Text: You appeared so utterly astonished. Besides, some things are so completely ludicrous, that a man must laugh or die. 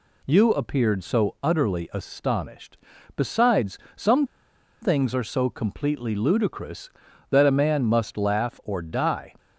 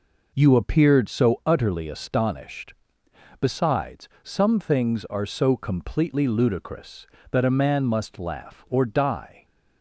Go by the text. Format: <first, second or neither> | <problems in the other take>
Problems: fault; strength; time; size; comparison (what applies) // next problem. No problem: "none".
second | pauses between "some" and "things"; noticeable; at 4.2 s; 0.57 s long